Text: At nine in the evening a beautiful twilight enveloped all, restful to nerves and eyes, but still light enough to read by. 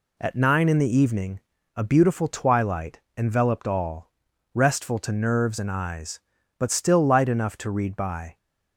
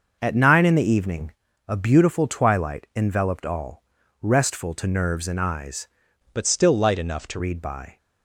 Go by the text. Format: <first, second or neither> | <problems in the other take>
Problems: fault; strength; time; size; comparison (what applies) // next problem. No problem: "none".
first | starts louder than the rest; noticeable; until 1.2 s; 6 dB // pauses between "evening" and "a"; slight; at 1.3 s; 0.36 s long; slight in the first // changes voice from "but" to "to"; from 6.3 to 7.3 s; 1.0 s long